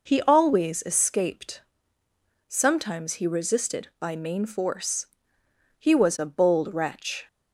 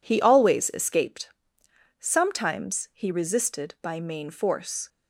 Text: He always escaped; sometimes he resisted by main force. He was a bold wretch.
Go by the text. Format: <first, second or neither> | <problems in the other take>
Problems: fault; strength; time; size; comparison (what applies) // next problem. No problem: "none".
first | stops before "He was a bold wretch"; at 4.8 s